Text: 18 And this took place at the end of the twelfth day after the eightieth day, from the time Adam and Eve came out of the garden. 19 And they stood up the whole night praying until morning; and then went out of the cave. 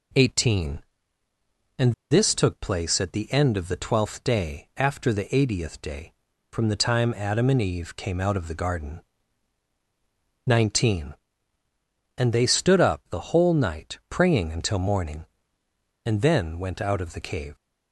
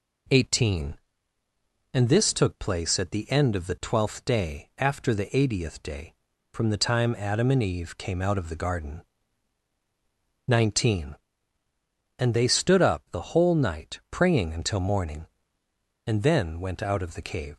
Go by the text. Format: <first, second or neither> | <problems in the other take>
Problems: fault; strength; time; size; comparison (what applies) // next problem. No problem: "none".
second | pauses between "And" and "this"; slight; at 1.9 s; 0.16 s long